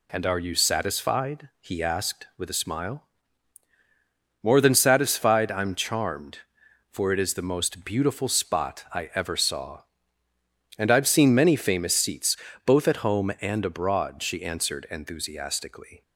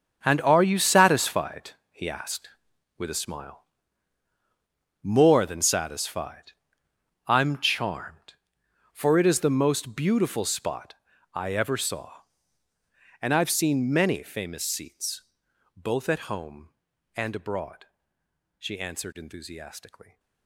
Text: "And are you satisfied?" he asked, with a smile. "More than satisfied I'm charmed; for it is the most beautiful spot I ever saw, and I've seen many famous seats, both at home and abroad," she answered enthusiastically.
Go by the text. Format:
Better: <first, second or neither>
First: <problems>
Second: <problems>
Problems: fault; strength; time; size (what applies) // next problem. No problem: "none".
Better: first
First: none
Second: gets quieter; strong; throughout; 13 dB // pauses between "satisfied" and "I'm"; noticeable; at 6.5 s; 0.74 s long // pauses between "spot" and "I"; at 10.9 s; 0.38 s long